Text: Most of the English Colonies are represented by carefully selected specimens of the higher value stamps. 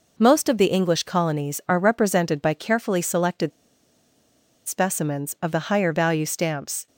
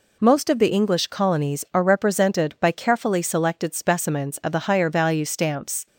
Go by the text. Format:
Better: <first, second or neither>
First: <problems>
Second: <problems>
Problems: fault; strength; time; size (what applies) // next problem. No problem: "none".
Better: second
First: pauses between "selected" and "specimens"; at 3.5 s; 1.1 s long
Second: none